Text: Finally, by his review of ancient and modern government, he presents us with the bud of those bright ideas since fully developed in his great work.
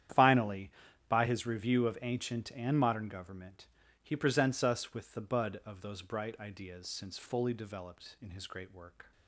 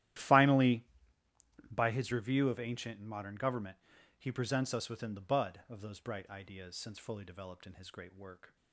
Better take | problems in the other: first | starts louder than the rest; strong; until 2.0 s; 13 dB; strong in the first // says "within" for "with"; at 4.8 s

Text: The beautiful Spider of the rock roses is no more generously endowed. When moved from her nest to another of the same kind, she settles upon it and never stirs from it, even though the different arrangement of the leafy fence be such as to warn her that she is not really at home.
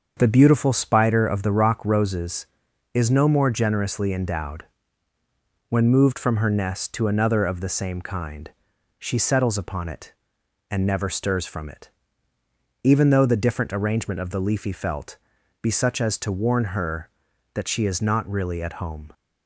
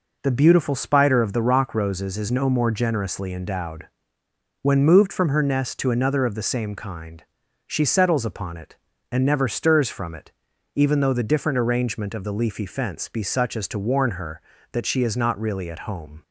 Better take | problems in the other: second | starts louder than the rest; until 1.1 s; 6.5 dB // says "felt" for "fence"; at 14.7 s

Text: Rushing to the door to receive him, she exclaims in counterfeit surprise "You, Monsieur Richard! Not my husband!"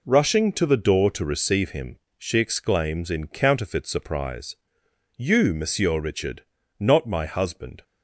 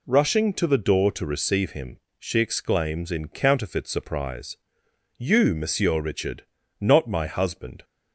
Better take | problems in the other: second | gets quieter; throughout; 7 dB // pauses between "surprise" and "You"; noticeable; at 4.5 s; 0.60 s long; noticeable in the second

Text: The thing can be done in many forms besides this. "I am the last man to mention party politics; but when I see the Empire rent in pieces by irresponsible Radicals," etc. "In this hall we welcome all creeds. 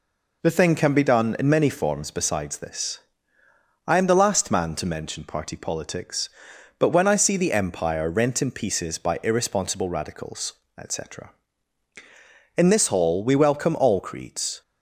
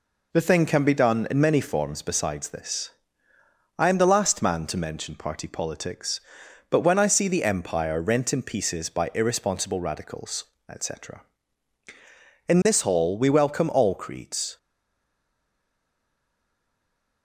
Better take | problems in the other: first | stays silent after the last word; strong; from 14.5 s on; 2.7 s long

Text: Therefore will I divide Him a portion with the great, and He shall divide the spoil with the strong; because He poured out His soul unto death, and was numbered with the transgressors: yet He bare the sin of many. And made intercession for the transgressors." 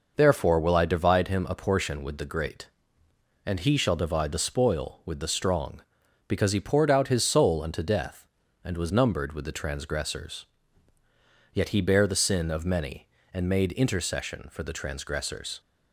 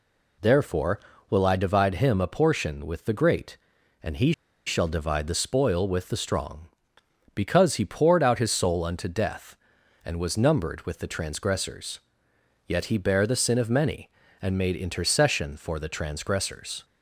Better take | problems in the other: first | pauses between "He" and "shall"; slight; at 4.3 s; 0.34 s long

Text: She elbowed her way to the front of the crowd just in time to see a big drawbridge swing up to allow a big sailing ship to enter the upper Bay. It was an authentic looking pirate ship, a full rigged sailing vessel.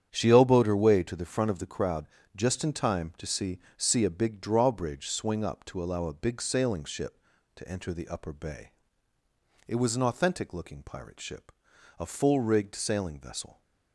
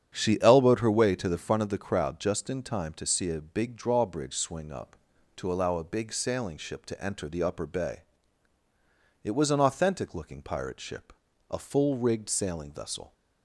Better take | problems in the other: second | starts louder than the rest; strong; until 1.1 s; 9 dB; strong in the second // pauses between "crowd" and "just"; slight; at 2.0 s; 0.28 s long // says "see" twice; at 3.7 s

